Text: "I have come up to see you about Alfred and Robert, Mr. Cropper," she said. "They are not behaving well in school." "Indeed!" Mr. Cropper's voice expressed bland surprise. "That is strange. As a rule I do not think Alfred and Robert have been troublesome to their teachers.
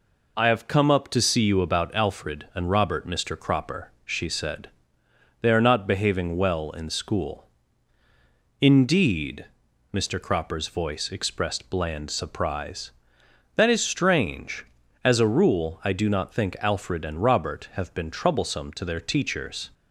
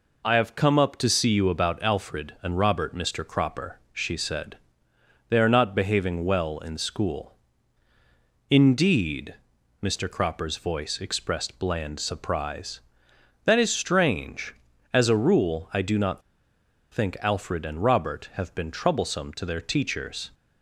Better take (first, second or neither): first